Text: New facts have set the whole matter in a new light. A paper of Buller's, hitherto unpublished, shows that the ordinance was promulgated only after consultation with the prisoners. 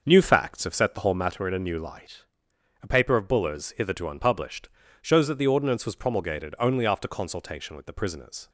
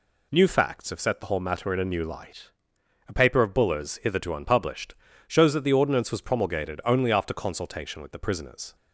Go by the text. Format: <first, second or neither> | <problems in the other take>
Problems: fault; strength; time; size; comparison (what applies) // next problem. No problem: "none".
second | starts louder than the rest; noticeable; until 1.3 s; 6 dB